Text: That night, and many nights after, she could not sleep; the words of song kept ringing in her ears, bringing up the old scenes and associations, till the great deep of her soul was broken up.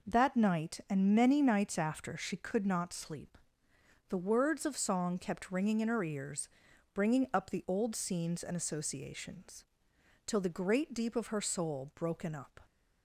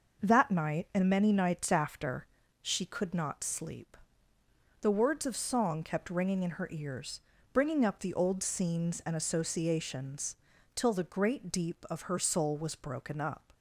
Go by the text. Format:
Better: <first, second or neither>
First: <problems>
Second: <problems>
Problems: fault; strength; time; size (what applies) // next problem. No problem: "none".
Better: second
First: skips "was"; at 11.9 s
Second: none